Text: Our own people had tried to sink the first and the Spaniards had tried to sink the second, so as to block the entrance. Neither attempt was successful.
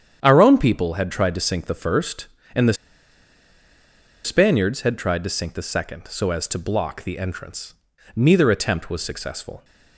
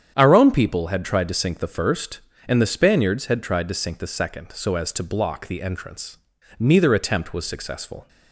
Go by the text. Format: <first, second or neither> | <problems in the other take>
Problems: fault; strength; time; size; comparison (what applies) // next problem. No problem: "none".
second | starts louder than the rest; strong; until 1.2 s; 8.5 dB; strong in the second // pauses between "the" and "Spaniards"; strong; at 2.7 s; 1.5 s long